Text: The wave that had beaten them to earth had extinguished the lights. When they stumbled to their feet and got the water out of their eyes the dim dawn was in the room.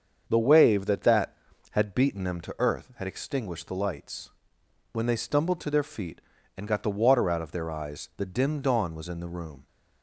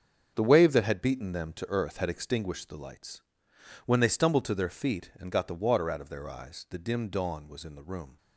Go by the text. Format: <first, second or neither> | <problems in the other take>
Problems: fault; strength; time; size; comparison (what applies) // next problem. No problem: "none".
second | starts louder than the rest; until 1.2 s; 7 dB; also in the second // says "that" twice; at 1.0 s